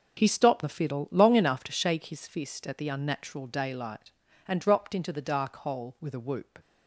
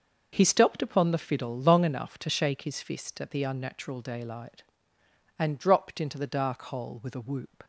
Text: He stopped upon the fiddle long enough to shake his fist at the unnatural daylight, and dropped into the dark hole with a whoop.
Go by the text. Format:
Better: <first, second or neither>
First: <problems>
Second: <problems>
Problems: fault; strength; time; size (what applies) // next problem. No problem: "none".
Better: second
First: starts louder than the rest; until 1.2 s; 6.5 dB // skips "upon"; at 0.6 s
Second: none